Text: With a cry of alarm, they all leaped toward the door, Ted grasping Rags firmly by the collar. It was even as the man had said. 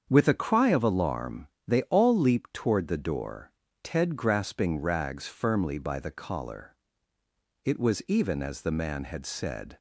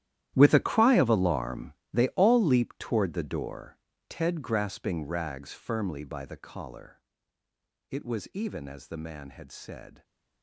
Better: first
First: starts louder than the rest; strong; until 1.1 s; 7 dB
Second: gets quieter; strong; throughout; 16 dB // starts louder than the rest; strong; until 1.3 s; 12.5 dB

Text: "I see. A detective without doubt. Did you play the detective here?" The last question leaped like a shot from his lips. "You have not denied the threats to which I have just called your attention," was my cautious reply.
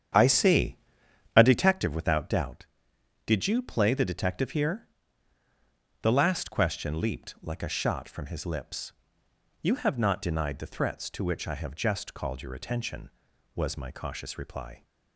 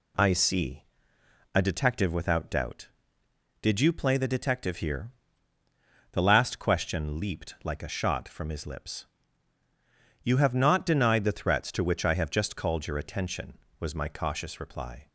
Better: second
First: starts louder than the rest; strong; until 1.8 s; 9 dB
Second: none

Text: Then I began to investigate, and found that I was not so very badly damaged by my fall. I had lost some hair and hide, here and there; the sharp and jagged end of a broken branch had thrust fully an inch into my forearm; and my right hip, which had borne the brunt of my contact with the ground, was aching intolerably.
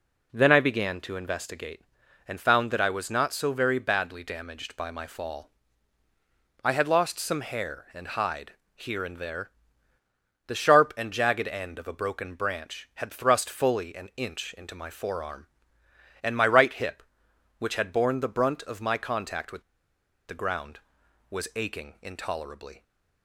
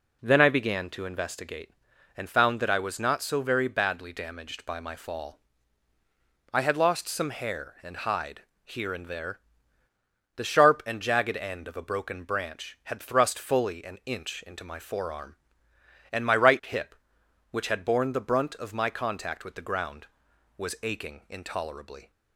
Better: second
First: pauses between "with" and "the"; noticeable; at 19.6 s; 0.66 s long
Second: none

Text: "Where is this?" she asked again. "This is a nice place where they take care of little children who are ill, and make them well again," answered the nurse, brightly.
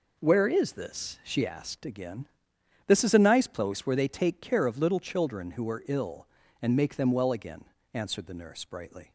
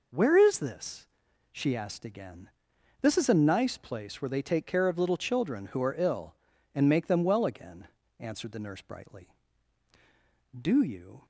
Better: first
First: none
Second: goes on to say "Do you"; noticeable; from 10.5 s on; 0.66 s long

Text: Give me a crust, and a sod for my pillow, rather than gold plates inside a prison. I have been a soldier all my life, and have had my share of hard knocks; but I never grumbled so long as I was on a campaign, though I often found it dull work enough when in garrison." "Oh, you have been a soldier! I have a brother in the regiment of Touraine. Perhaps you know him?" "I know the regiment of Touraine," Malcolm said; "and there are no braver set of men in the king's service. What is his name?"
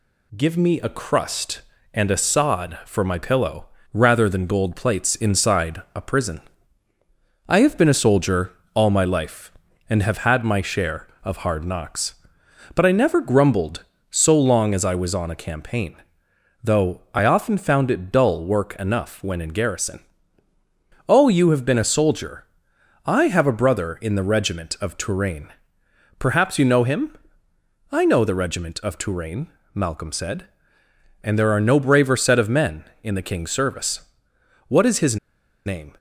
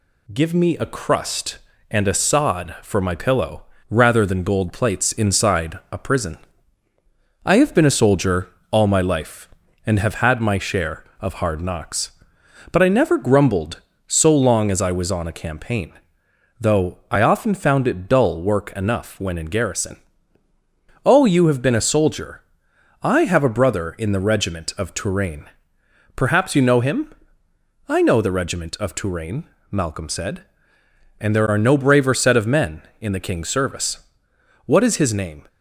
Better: second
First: pauses between "soldier" and "all"; slight; at 8.5 s; 0.24 s long // pauses between "his" and "name"; noticeable; at 35.1 s; 0.50 s long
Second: pauses between "soldier" and "all"; slight; at 8.4 s; 0.24 s long

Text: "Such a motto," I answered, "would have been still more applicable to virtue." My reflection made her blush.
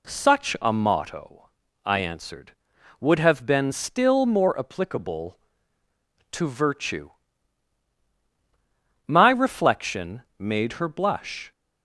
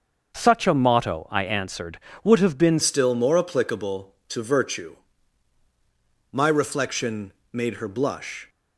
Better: first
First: pauses between "reflection" and "made"; slight; at 10.2 s; 0.16 s long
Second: starts louder than the rest; until 1.3 s; 6.5 dB // changes voice at "still"; from 2.8 s on; 5.6 s long // pauses between "reflection" and "made"; slight; at 7.3 s; 0.22 s long

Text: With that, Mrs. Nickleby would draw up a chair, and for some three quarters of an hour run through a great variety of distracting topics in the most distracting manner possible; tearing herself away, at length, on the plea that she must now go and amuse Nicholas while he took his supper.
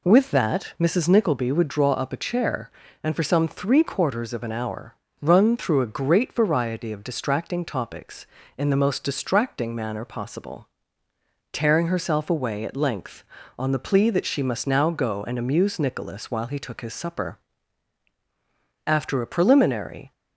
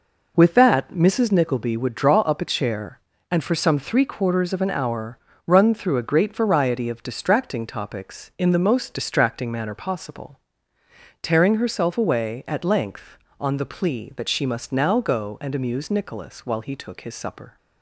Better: second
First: pauses between "hour" and "run"; slight; at 4.9 s; 0.26 s long // goes on to say "After a preliminary"; noticeable; from 18.8 s on; 1.2 s long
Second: pauses between "hour" and "run"; slight; at 5.1 s; 0.30 s long

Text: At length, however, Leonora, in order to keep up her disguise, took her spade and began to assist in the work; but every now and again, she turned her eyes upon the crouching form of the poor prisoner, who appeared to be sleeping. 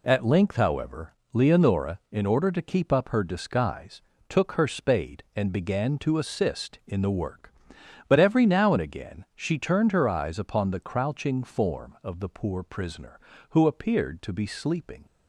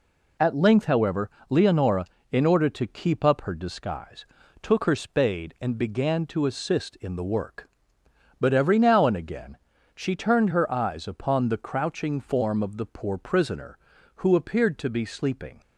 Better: neither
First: none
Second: none

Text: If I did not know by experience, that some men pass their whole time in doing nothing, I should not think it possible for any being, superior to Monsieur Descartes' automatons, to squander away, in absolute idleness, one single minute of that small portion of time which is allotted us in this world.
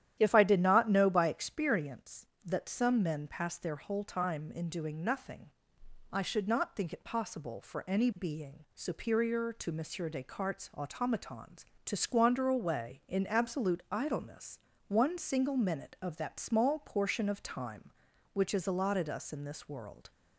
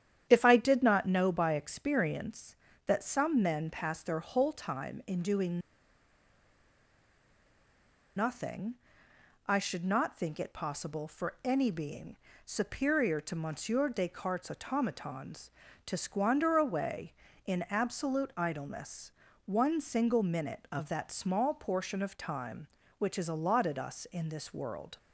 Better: first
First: starts louder than the rest; strong; until 1.2 s; 11 dB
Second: starts louder than the rest; strong; until 1.3 s; 10 dB // pauses between "doing" and "nothing"; strong; at 5.6 s; 2.5 s long

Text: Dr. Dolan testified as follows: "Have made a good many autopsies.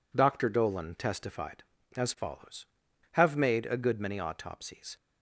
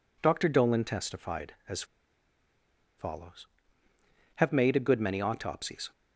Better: first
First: none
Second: pauses between "as" and "follows"; at 1.8 s; 1.1 s long

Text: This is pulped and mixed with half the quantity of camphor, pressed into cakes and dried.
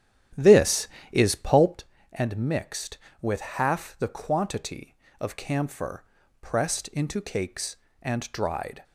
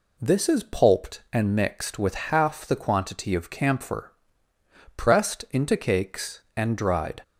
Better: second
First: starts louder than the rest; strong; until 1.8 s; 10.5 dB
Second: none

